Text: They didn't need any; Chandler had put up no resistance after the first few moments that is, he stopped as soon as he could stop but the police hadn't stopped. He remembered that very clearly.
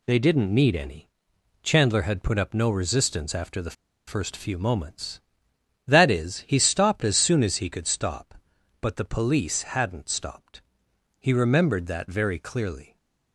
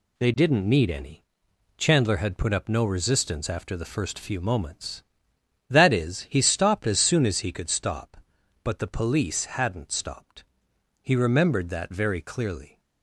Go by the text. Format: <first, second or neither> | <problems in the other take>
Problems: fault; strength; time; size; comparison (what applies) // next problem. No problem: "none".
second | pauses between "the" and "first"; slight; at 3.7 s; 0.33 s long